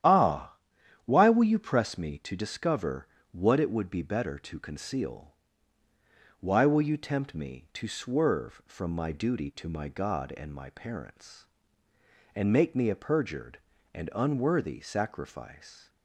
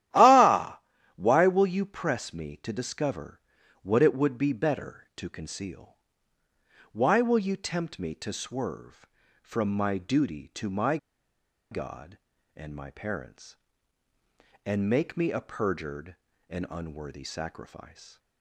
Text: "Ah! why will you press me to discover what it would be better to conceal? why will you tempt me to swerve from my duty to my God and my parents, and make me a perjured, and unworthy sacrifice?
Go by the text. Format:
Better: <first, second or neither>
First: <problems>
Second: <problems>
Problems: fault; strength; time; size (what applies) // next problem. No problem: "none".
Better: first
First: starts louder than the rest; strong; until 1.5 s; 10.5 dB // pauses between "discover" and "what"; slight; at 3.0 s; 0.24 s long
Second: starts louder than the rest; strong; until 1.4 s; 12.5 dB // pauses between "discover" and "what"; at 3.3 s; 0.44 s long // pauses between "my" and "God"; noticeable; at 10.9 s; 0.74 s long